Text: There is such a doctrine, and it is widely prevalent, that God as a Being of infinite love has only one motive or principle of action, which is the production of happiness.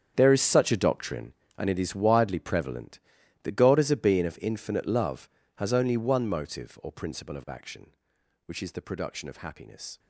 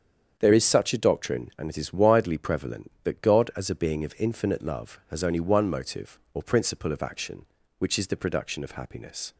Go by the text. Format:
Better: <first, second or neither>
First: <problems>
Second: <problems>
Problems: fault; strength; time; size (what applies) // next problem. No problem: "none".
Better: second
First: gets quieter; strong; throughout; 15 dB // starts louder than the rest; strong; until 1.1 s; 8 dB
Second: starts louder than the rest; strong; until 1.3 s; 7.5 dB